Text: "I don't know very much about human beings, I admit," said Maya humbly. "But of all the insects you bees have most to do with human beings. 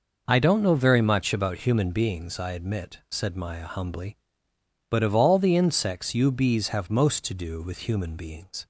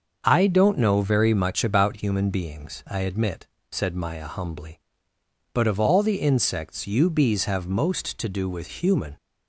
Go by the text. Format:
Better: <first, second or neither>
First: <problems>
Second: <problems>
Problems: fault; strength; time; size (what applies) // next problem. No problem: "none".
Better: first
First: none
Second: starts louder than the rest; until 1.2 s; 6.5 dB // stops before "beings"; at 9.1 s